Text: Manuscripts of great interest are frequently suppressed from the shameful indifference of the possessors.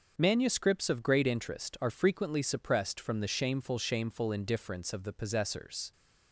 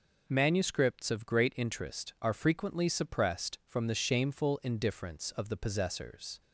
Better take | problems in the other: second | starts louder than the rest; until 1.1 s; 6.5 dB // says "shameful" twice; at 3.7 s

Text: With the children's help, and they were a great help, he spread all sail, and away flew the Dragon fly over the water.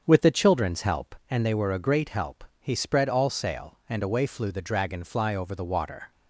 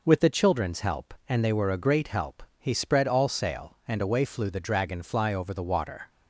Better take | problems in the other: second | starts louder than the rest; strong; until 1.2 s; 7.5 dB

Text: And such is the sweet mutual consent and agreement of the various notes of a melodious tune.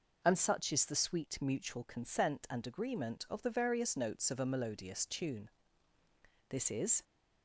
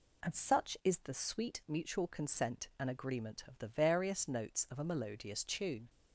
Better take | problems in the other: second | goes on to say "This is"; from 6.4 s on; 0.54 s long

